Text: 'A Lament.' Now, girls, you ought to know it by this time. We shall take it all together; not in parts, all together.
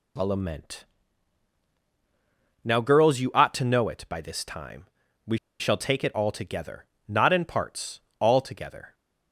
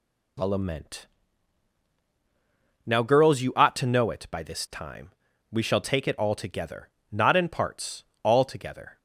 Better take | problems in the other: second | pauses between "We" and "shall"; slight; at 5.3 s; 0.23 s long

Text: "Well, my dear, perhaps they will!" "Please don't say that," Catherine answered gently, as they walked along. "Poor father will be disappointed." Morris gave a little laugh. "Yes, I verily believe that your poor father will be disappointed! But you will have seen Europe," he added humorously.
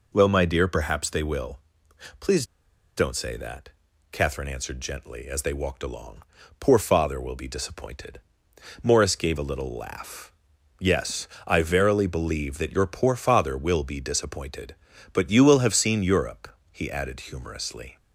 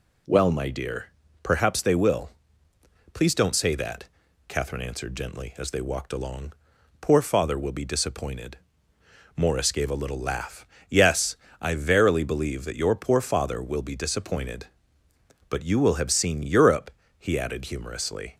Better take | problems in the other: second | pauses between "Please" and "don't"; noticeable; at 2.4 s; 0.52 s long

